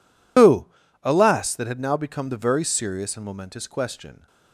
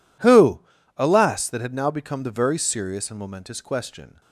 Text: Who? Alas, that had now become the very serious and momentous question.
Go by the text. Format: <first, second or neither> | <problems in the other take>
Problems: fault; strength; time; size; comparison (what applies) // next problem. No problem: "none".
second | loses the start of "Who"; at 0.3 s; 105 ms